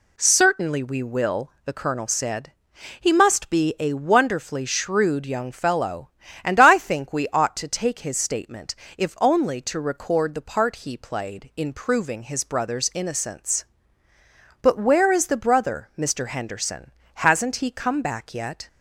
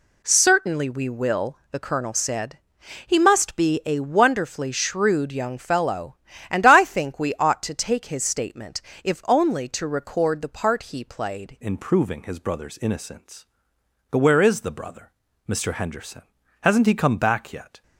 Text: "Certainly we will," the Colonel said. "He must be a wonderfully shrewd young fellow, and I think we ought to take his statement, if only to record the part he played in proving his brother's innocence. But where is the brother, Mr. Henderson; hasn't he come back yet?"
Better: first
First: none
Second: changes voice at "in"; from 11.6 s on; 6.2 s long

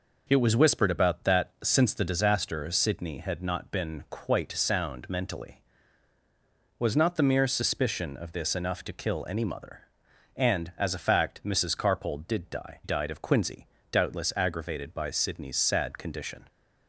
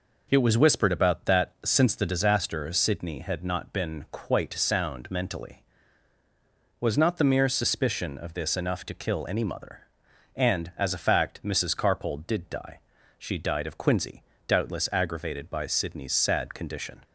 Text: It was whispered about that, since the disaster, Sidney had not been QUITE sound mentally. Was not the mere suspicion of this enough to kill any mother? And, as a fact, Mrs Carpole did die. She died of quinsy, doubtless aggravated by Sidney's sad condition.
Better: second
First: skips "She"; at 12.8 s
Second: none

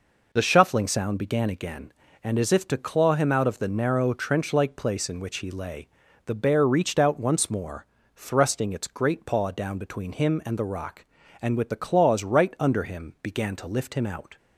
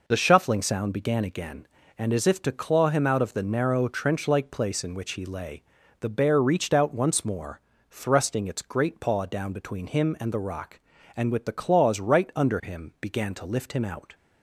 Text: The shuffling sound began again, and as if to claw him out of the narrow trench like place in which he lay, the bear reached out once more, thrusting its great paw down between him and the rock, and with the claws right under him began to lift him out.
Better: neither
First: none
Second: none

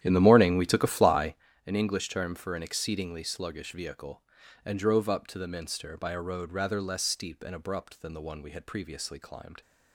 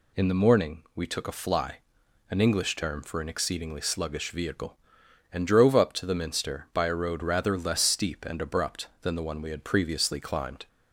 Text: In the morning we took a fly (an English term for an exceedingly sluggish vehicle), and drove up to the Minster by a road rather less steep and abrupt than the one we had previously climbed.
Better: second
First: starts louder than the rest; strong; until 1.5 s; 11 dB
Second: none

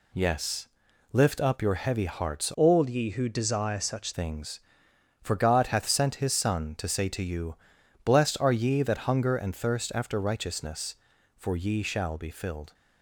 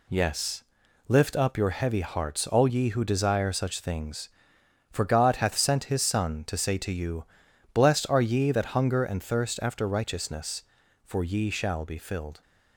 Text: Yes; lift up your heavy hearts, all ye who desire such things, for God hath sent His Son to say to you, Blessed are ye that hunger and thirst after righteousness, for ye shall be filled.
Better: second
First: changes voice from "all" to "such"; from 2.5 to 4.1 s; 1.6 s long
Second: none

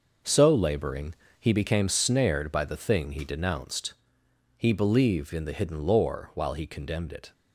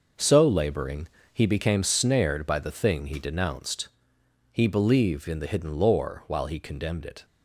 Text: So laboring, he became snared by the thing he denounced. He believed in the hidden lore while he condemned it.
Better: neither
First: none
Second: none

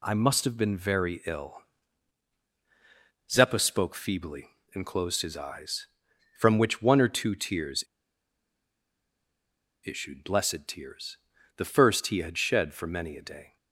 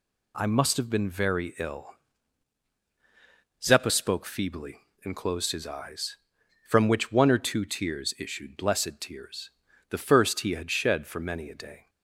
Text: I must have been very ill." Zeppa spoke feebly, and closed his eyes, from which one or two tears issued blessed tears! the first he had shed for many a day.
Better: second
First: pauses between "tears" and "issued"; strong; at 7.8 s; 1.9 s long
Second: none

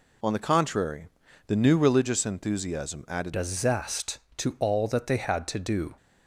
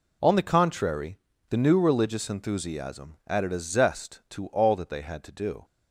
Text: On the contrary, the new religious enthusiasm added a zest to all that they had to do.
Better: second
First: changes voice at "a"; from 3.3 s on; 2.6 s long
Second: none

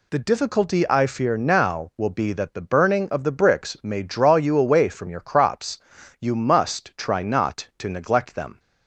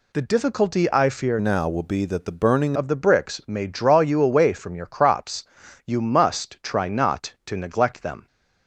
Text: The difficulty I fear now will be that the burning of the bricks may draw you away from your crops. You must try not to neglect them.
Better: first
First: none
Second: changes voice from "now" to "burning"; from 1.3 to 2.7 s; 1.4 s long

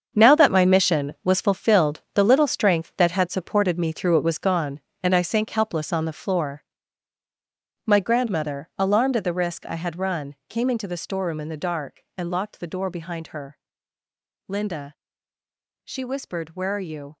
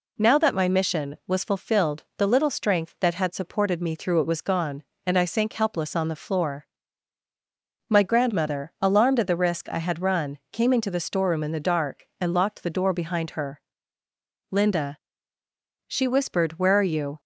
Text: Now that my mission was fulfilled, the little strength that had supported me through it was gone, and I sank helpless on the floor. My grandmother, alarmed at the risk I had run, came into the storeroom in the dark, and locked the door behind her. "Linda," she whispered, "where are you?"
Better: second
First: gets quieter; strong; throughout; 12.5 dB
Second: none

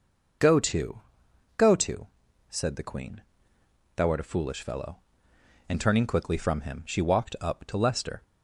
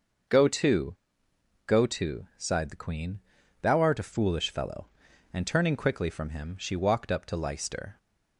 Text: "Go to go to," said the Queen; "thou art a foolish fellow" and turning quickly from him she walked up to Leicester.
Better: first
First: pauses between "to" and "go"; noticeable; at 1.0 s; 0.56 s long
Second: starts louder than the rest; until 2.0 s; 6 dB // pauses between "to" and "go"; noticeable; at 0.9 s; 0.70 s long // says "sighed" for "said"; at 2.3 s

